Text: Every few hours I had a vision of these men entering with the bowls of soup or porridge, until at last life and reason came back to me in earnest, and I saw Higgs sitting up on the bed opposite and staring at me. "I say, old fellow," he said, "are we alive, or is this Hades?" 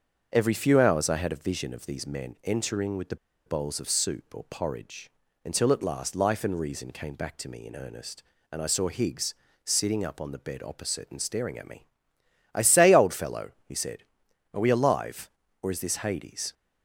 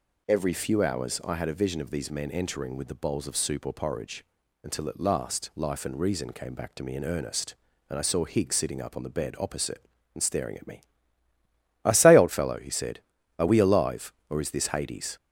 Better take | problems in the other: second | starts louder than the rest; until 1.3 s; 6.5 dB // pauses between "the" and "bowls"; slight; at 3.1 s; 0.31 s long // pauses between "Higgs" and "sitting"; slight; at 9.3 s; 0.32 s long

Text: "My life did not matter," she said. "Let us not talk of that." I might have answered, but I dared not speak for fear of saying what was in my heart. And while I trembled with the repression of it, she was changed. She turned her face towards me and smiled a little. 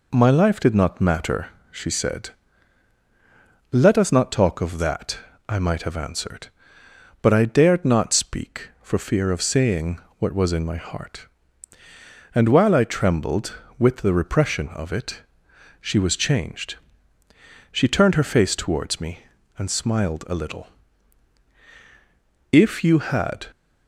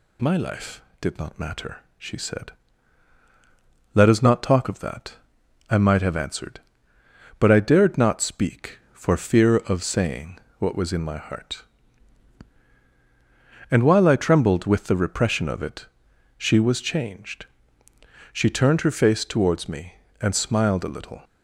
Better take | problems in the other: second | pauses between "saying" and "what"; slight; at 10.0 s; 0.18 s long; slight in the second // goes on to say "If you had"; noticeable; from 22.5 s on; 0.96 s long

